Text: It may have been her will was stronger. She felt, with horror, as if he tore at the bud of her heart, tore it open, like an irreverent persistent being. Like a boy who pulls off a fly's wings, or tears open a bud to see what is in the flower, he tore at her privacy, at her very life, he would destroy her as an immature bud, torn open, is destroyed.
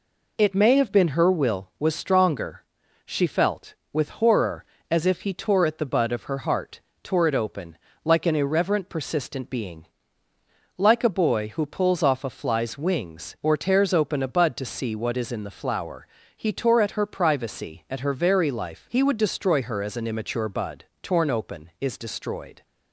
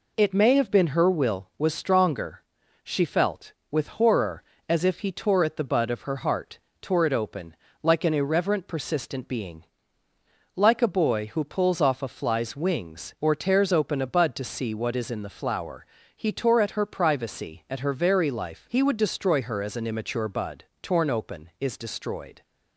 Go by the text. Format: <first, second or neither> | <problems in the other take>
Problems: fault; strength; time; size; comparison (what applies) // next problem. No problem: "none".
neither | none